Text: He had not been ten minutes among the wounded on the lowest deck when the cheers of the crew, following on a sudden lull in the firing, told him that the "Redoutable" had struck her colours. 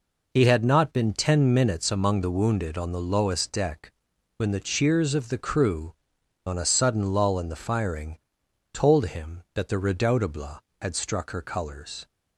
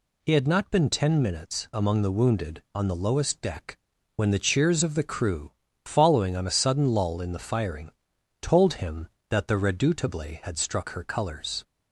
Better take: second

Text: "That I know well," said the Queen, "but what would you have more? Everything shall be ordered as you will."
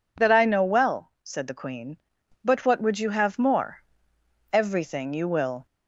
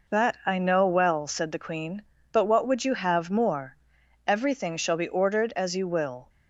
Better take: second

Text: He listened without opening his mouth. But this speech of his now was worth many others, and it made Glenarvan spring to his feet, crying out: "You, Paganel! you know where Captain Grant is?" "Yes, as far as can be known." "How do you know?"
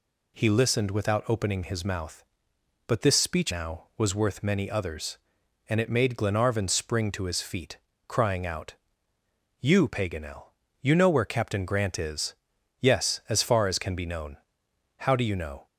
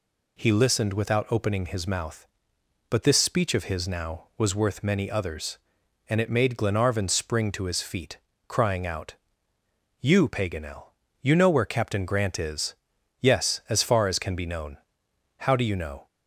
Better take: second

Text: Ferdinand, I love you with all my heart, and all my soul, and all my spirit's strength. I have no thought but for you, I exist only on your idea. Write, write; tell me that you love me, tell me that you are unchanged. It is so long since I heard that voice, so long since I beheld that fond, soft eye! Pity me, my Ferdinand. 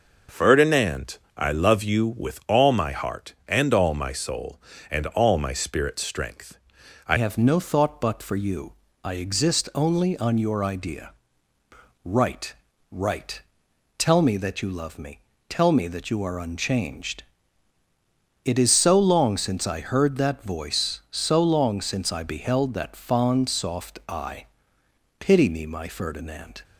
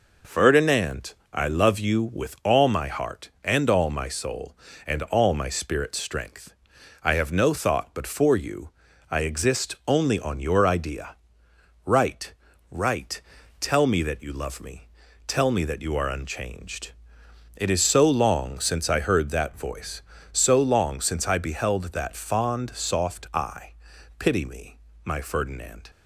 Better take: second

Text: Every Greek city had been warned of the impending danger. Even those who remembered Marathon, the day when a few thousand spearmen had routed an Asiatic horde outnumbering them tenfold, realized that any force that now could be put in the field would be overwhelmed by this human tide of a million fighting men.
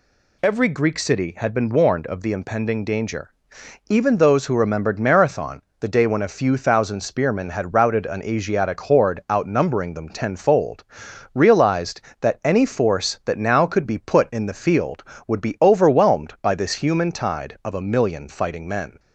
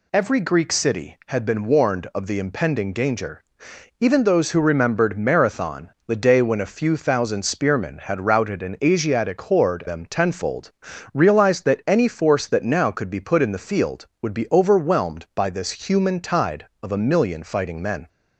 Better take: first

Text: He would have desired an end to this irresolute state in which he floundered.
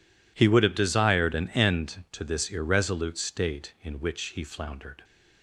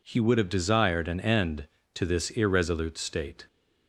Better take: first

